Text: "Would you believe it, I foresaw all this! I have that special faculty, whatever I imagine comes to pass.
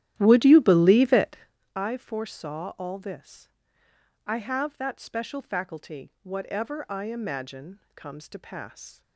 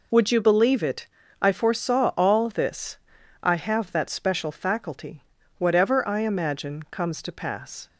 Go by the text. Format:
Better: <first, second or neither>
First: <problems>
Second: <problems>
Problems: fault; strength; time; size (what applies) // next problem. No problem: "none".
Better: second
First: starts louder than the rest; strong; until 1.6 s; 12.5 dB // pauses between "imagine" and "comes"; slight; at 7.7 s; 0.16 s long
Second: none